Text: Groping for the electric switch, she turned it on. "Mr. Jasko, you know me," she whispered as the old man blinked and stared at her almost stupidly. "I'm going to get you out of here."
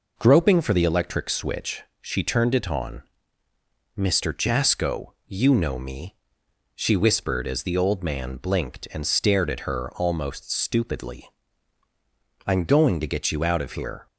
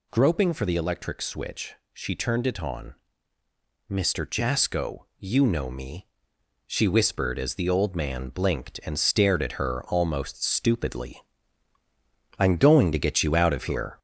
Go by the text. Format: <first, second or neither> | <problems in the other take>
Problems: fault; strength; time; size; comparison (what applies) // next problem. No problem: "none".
first | gets louder; noticeable; throughout; 4 dB